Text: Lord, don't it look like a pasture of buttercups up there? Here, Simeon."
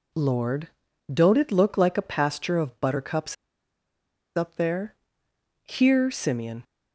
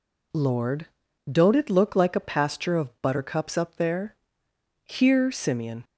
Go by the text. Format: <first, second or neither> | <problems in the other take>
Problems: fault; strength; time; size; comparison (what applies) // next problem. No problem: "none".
second | pauses between "buttercups" and "up"; at 3.3 s; 1.0 s long